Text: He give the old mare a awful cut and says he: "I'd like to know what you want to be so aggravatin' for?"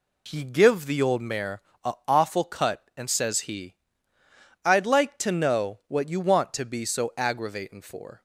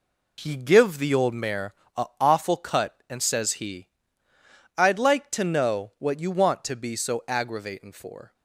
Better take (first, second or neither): first